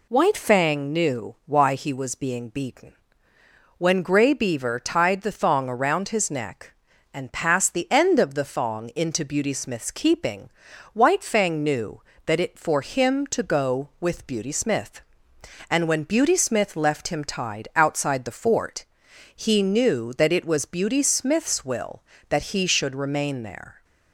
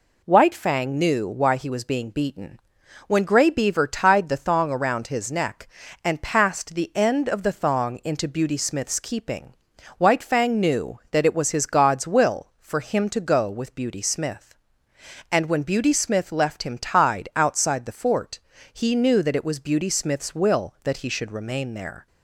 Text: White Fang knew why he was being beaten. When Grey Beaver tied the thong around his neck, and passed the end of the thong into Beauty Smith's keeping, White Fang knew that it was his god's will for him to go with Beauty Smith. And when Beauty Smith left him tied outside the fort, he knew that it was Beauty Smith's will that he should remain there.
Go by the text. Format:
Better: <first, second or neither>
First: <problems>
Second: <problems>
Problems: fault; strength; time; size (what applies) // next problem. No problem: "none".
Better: second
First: skips "was his god's will"; at 12.5 s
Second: none